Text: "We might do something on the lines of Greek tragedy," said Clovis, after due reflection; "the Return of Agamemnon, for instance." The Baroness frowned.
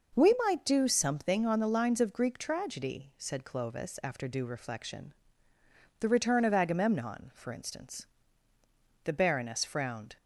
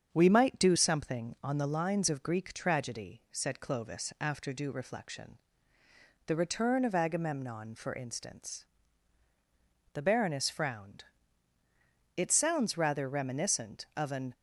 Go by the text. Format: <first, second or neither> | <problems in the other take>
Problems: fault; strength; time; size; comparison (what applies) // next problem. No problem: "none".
first | starts louder than the rest; strong; until 1.1 s; 7.5 dB // goes on to say "It sounds rather reminiscent of an"; strong; from 12.1 s on; 2.1 s long